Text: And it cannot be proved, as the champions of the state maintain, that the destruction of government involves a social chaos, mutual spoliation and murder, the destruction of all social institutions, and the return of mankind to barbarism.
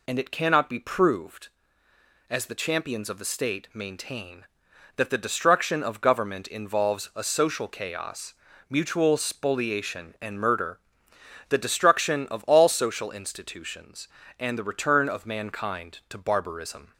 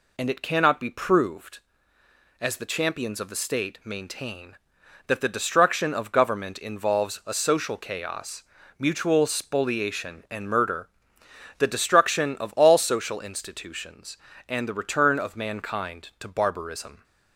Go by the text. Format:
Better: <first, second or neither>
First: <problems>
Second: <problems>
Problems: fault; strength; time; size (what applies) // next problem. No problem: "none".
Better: neither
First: none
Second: none